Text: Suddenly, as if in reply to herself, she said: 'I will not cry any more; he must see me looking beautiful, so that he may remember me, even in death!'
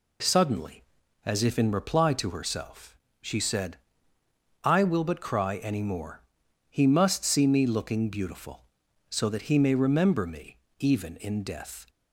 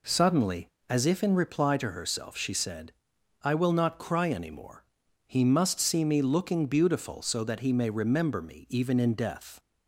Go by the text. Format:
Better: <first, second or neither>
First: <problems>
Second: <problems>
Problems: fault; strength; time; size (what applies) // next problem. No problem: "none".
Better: second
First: says "but" for "not"; at 5.0 s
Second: none